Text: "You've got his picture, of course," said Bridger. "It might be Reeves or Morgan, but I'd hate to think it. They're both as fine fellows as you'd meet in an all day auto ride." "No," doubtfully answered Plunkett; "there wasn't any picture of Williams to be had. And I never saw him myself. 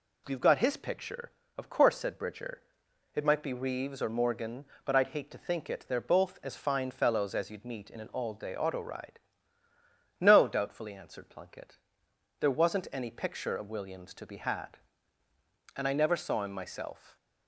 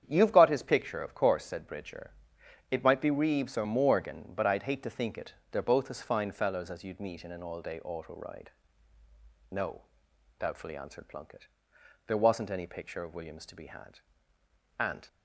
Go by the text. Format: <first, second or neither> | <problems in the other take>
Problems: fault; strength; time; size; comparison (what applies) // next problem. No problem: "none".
first | starts louder than the rest; strong; until 1.0 s; 8.5 dB // stops before "I never saw him myself"; at 15.0 s